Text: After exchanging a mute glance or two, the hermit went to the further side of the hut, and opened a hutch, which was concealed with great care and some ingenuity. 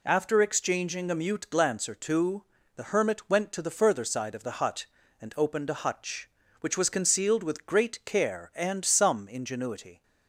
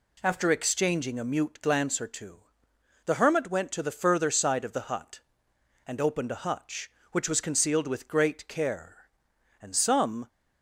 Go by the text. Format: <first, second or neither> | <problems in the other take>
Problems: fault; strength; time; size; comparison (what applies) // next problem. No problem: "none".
first | stops before "ingenuity"; at 10.2 s